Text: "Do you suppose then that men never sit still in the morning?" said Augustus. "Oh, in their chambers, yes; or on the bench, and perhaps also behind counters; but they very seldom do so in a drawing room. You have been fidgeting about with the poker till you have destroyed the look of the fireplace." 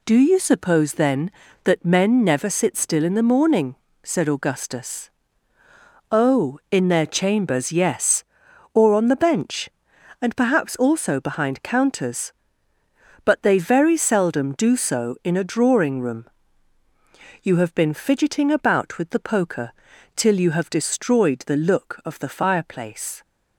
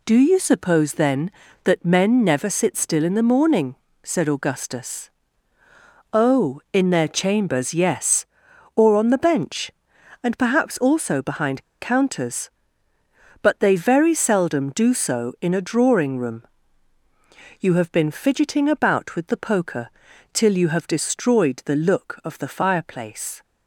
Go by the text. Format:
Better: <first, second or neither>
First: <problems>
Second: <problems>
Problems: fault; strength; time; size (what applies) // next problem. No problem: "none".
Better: first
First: pauses between "poker" and "till"; at 19.7 s; 0.42 s long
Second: pauses between "behind" and "counters"; slight; at 11.6 s; 0.15 s long // pauses between "poker" and "till"; at 19.9 s; 0.42 s long